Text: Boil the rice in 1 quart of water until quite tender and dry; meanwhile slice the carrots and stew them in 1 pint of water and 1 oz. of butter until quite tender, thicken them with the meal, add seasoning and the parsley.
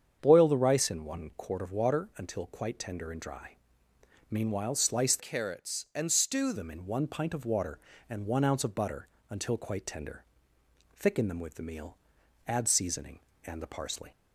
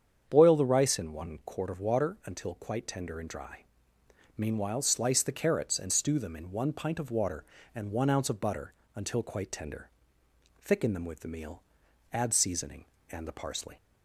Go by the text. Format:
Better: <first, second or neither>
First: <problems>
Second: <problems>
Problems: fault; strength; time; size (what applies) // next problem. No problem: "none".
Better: second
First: starts louder than the rest; strong; until 1.2 s; 7.5 dB // changes voice from "carrots" to "stew"; from 5.1 to 6.5 s; 1.4 s long // pauses between "butter" and "until"; slight; at 9.0 s; 0.22 s long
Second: starts louder than the rest; strong; until 1.3 s; 8 dB // pauses between "butter" and "until"; slight; at 8.7 s; 0.22 s long